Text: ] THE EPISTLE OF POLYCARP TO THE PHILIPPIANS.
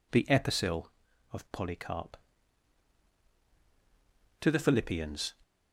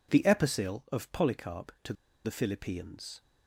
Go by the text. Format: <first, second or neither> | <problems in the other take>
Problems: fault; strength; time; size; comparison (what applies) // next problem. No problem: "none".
first | pauses between "TO" and "THE"; slight; at 1.9 s; 0.31 s long